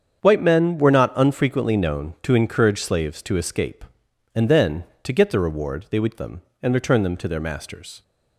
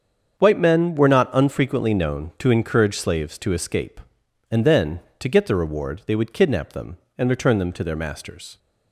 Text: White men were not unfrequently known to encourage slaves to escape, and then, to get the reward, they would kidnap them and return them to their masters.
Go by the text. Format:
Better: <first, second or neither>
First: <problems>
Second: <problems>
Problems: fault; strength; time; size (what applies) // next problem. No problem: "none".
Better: second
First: starts louder than the rest; strong; until 1.2 s; 7.5 dB // skips "kidnap"; at 6.1 s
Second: starts louder than the rest; strong; until 1.4 s; 7 dB